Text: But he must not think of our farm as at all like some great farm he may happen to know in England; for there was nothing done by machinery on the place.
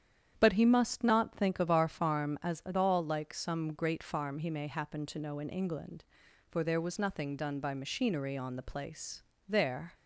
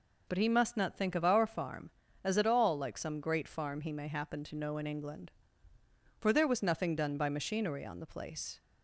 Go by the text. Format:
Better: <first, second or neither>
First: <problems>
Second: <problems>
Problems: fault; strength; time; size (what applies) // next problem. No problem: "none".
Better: second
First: starts louder than the rest; strong; until 1.3 s; 9 dB // goes on to say "There"; slight; from 9.4 s on; 0.46 s long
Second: none